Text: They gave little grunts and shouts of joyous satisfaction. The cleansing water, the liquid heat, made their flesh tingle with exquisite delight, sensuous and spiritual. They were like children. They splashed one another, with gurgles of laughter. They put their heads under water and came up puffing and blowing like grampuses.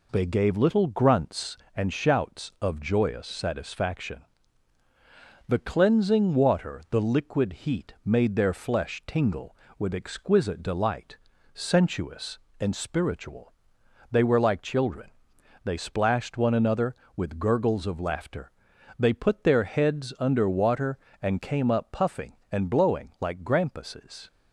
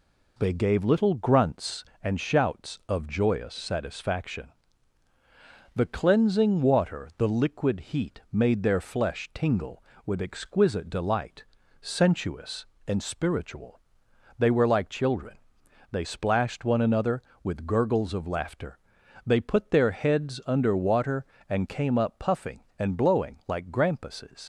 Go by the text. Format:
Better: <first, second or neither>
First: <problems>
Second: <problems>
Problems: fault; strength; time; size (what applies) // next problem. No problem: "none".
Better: first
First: none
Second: leaves "grampuses" unfinished; at 24.4 s; 65 ms